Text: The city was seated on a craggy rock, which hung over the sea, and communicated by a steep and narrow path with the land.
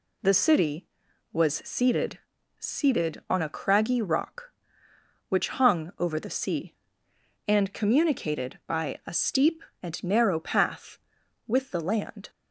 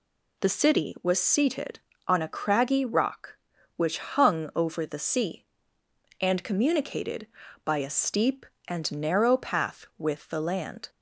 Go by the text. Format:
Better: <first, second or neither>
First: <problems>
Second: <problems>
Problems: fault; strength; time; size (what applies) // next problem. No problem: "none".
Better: second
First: says "seated" twice; at 2.6 s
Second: none